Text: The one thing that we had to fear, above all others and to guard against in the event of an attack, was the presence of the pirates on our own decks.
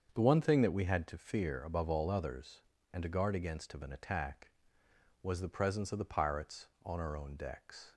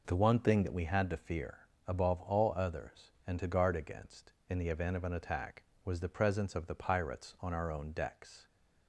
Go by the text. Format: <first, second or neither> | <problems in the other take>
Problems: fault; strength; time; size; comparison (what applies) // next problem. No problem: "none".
second | starts louder than the rest; until 1.1 s; 7 dB // skips "in the event"; at 3.7 s